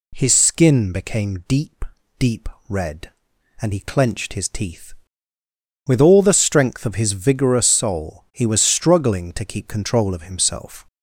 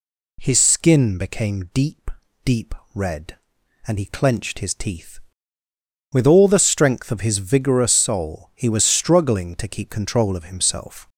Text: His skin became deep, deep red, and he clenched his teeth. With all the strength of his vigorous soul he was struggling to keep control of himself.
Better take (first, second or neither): neither